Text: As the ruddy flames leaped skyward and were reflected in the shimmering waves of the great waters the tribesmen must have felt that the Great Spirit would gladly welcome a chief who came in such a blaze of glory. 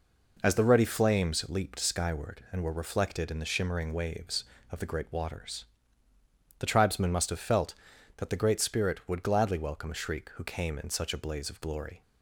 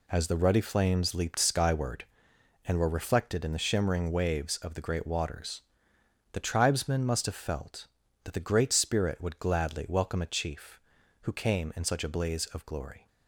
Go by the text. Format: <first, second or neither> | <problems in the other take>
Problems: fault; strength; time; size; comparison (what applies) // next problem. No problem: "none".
second | pauses between "waters" and "the"; noticeable; at 5.6 s; 0.96 s long; noticeable in the second // says "shriek" for "chief"; at 9.9 s